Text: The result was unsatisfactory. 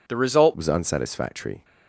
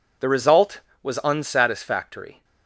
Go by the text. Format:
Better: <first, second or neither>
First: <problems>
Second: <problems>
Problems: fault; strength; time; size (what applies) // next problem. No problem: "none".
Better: second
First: changes voice at "was"; from 0.5 s on; 1.1 s long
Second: none